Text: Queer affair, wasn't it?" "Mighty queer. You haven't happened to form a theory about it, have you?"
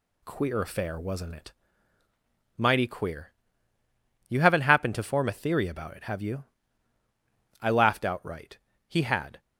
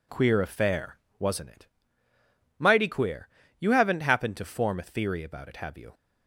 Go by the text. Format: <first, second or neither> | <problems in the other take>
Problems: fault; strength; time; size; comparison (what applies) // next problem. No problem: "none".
second | goes on to say "I laughed outright He had"; strong; from 7.5 s on; 1.8 s long